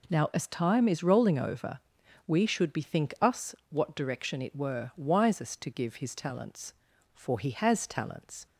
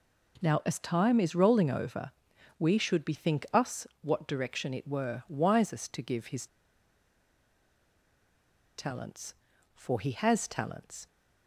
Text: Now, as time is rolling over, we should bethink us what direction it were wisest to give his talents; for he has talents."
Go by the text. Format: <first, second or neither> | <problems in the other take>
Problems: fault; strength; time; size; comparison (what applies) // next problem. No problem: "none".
first | pauses between "us" and "what"; slight; at 3.8 s; 0.16 s long; slight in the first // pauses between "his" and "talents"; strong; at 6.4 s; 2.3 s long